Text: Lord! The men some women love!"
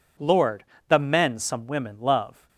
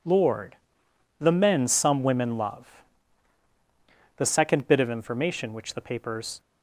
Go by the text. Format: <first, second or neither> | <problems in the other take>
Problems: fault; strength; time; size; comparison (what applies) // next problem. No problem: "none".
first | goes on to say "The second bit of information which the papers"; strong; from 4.1 s on; 2.2 s long